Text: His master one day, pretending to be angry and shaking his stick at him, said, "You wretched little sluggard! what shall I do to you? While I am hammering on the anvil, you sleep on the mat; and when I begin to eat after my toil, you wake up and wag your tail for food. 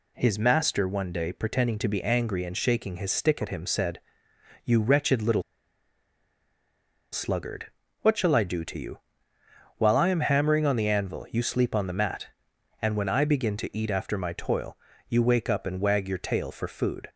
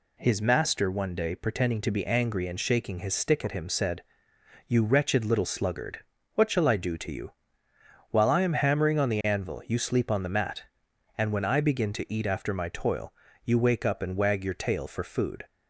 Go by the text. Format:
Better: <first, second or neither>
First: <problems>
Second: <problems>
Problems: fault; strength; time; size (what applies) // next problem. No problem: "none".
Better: second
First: pauses between "little" and "sluggard"; strong; at 5.4 s; 1.7 s long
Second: none